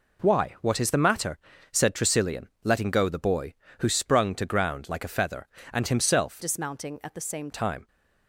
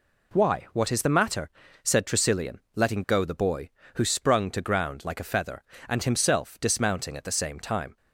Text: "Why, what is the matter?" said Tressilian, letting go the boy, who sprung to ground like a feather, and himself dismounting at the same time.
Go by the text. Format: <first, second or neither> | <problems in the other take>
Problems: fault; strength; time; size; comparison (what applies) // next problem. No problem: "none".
second | changes voice from "dismounting" to "same"; from 6.4 to 7.4 s; 1.0 s long